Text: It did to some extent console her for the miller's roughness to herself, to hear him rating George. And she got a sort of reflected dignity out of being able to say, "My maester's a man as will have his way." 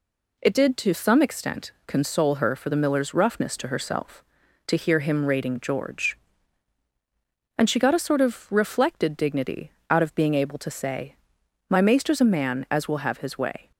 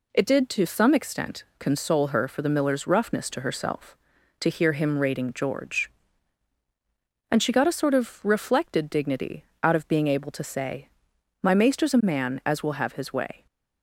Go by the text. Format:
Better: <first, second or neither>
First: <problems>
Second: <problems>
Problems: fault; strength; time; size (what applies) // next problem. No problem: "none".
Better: neither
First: pauses between "dignity" and "out"; slight; at 9.7 s; 0.18 s long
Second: pauses between "dignity" and "out"; slight; at 9.4 s; 0.18 s long